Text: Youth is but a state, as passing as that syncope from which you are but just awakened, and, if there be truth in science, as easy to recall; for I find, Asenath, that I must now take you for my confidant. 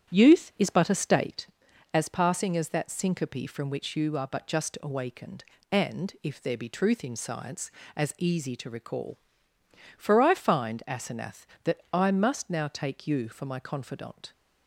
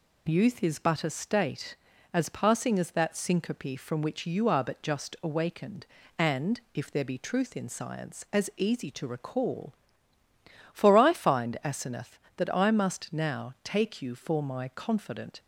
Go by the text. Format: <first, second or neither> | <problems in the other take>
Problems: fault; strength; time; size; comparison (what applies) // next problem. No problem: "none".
second | starts louder than the rest; strong; until 1.5 s; 9.5 dB